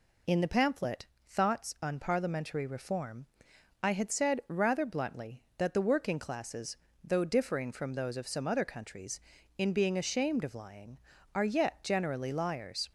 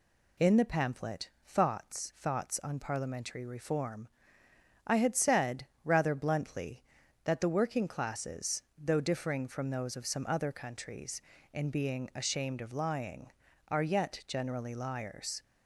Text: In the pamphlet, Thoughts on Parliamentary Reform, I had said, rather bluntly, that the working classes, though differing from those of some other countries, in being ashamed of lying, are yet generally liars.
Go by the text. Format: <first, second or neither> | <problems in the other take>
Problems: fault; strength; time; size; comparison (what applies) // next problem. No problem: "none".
first | says "Thoughts" twice; at 2.1 s